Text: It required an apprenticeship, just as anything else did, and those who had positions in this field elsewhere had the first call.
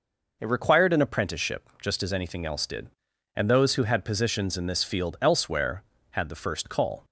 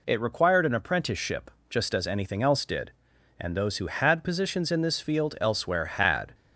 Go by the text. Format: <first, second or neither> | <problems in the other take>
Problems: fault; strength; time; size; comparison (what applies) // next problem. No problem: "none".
first | stops before "the first call"; at 6.3 s